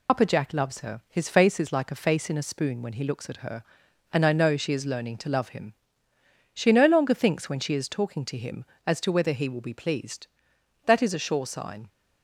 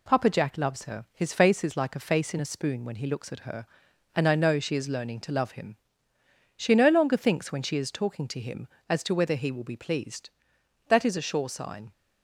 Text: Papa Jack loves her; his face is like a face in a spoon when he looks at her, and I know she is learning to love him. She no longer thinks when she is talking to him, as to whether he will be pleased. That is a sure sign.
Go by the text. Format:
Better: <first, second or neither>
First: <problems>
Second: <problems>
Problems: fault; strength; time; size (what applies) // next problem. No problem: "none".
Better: second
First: loses the start of "Papa"; at 0.0 s; 80 ms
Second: none